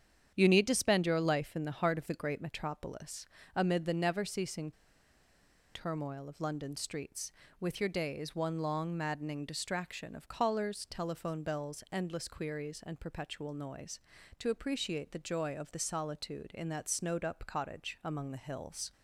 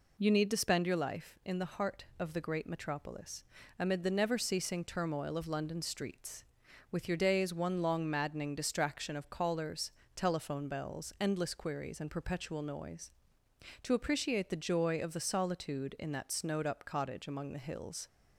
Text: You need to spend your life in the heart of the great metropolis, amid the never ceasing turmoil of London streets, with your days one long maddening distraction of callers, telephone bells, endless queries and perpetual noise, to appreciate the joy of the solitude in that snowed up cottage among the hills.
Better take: second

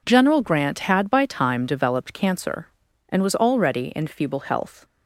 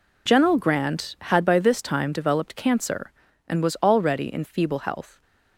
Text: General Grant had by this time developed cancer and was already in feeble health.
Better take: second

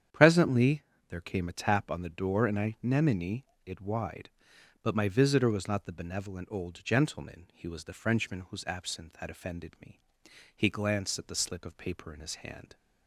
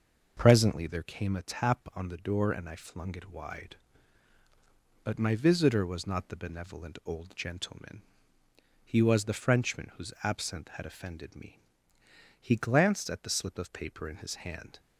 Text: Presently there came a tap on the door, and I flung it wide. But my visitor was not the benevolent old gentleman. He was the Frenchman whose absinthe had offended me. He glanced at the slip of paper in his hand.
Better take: second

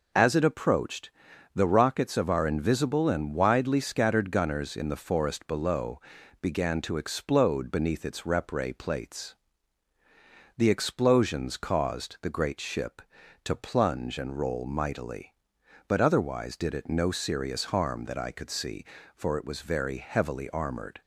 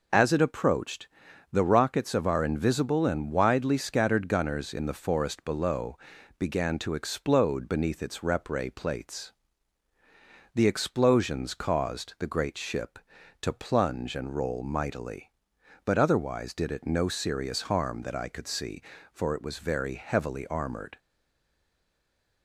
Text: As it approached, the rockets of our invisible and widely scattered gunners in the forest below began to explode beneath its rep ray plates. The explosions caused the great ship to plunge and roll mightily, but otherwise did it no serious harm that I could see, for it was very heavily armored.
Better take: first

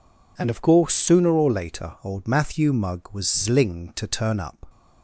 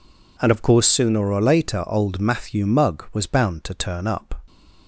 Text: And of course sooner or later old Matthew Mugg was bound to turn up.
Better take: second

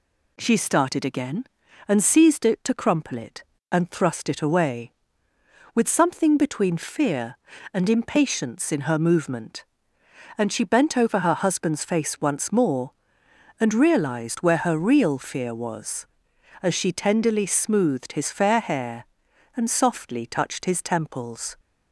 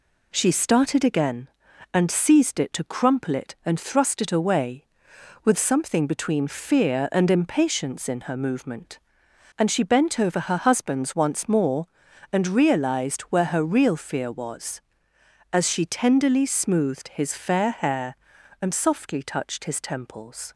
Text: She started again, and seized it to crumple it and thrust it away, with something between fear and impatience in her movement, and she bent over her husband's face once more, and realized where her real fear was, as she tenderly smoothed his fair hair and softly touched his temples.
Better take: first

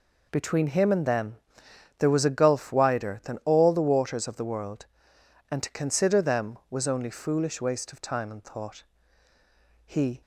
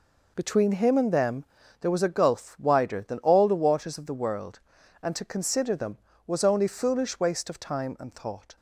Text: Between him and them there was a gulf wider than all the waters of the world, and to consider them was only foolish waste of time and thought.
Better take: second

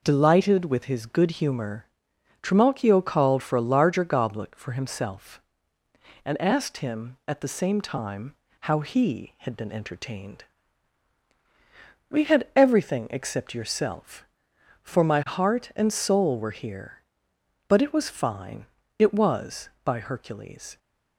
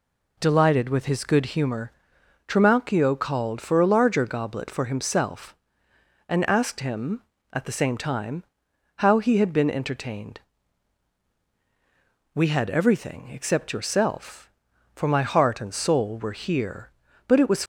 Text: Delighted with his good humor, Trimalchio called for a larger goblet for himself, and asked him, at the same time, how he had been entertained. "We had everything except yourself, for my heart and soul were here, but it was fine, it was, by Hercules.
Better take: first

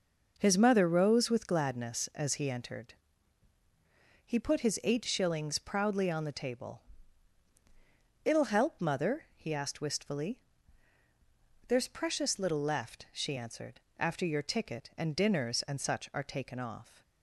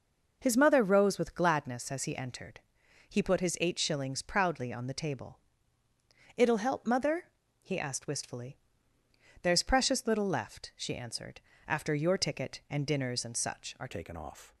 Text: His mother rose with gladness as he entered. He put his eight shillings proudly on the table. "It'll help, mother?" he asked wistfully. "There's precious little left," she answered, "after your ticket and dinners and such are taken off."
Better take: first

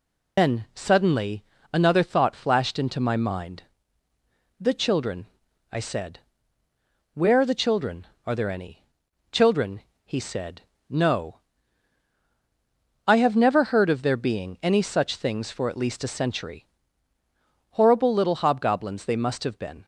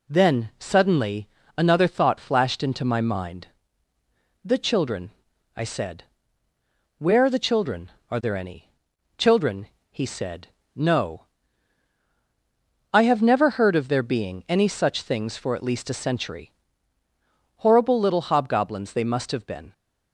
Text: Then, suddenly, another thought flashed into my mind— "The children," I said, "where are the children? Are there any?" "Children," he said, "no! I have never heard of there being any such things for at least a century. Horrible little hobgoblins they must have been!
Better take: second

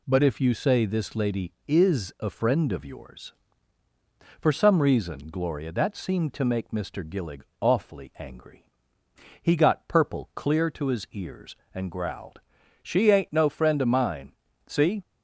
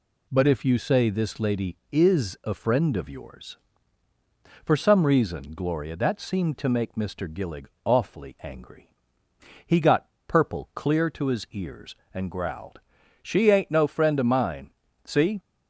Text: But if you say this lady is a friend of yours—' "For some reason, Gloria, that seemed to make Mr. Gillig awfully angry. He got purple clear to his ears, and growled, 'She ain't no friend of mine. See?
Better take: first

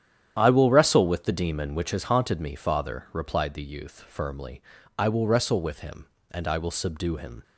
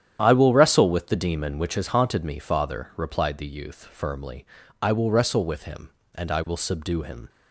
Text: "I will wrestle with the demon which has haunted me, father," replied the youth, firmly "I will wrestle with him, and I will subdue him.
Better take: neither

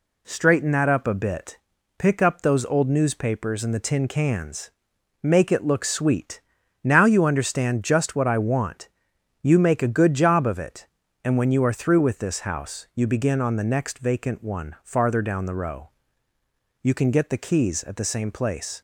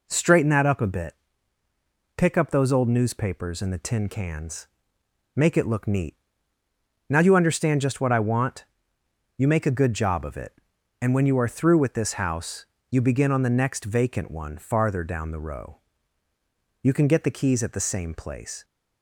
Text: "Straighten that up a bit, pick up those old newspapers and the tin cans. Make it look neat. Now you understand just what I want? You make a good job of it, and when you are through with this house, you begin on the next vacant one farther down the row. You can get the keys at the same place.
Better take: second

